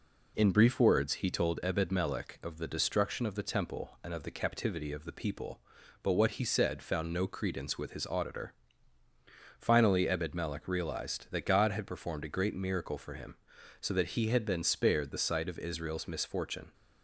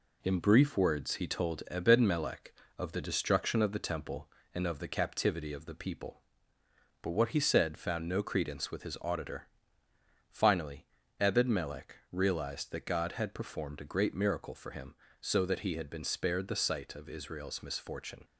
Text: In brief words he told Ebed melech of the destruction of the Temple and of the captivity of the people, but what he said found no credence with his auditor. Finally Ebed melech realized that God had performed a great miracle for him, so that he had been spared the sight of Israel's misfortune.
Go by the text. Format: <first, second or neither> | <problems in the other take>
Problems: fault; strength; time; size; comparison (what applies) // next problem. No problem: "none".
first | gets quieter; throughout; 4 dB // pauses between "Finally" and "Ebed"; slight; at 10.8 s; 0.34 s long // pauses between "melech" and "realized"; slight; at 11.9 s; 0.16 s long